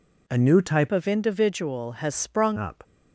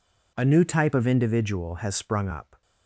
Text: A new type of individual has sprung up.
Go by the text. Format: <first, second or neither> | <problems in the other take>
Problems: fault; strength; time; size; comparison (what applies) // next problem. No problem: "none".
second | changes voice from "of" to "sprung"; from 0.9 to 2.5 s; 1.6 s long